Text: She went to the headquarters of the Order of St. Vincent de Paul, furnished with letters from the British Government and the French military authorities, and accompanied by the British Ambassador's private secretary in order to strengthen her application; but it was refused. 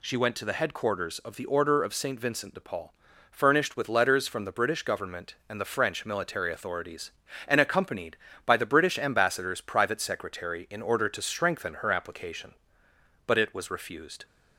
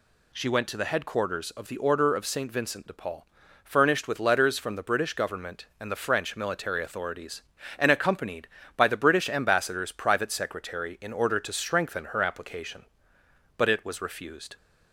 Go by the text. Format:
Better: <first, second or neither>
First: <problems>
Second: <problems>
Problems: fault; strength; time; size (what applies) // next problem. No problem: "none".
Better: neither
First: none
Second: none